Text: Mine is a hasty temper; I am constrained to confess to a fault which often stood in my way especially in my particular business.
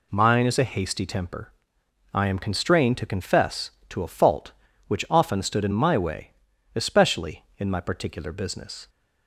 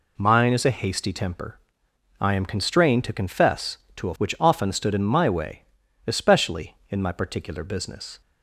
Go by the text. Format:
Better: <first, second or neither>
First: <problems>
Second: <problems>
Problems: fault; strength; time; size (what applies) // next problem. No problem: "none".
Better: first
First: pauses between "way" and "especially"; noticeable; at 6.2 s; 0.46 s long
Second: skips "fault"; at 4.1 s // pauses between "way" and "especially"; noticeable; at 5.6 s; 0.46 s long